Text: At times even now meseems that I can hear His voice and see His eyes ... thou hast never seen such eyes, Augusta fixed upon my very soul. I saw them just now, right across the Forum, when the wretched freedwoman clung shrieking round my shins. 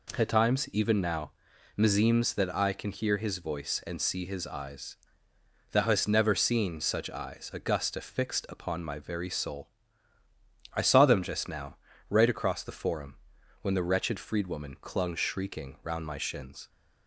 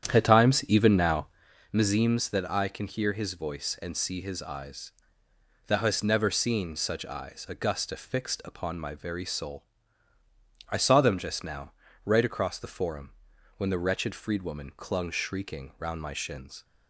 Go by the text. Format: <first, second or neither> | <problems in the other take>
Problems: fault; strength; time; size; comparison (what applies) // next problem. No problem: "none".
first | starts louder than the rest; strong; until 1.6 s; 9.5 dB // pauses between "now" and "meseems"; noticeable; at 1.2 s; 0.46 s long; noticeable in the first